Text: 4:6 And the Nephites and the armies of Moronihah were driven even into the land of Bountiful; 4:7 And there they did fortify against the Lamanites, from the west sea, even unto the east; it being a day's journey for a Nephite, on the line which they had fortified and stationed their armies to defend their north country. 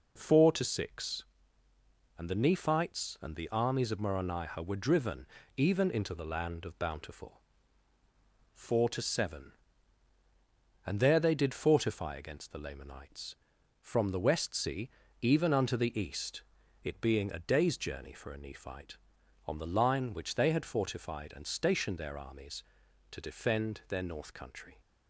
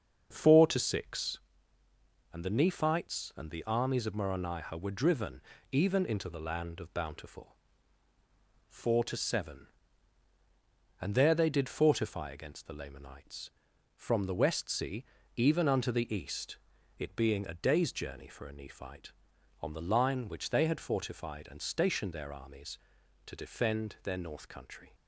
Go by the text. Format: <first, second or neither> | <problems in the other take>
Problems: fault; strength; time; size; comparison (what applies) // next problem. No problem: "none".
first | starts louder than the rest; until 1.5 s; 6.5 dB // pauses between "driven" and "even"; slight; at 5.4 s; 0.32 s long; slight in the first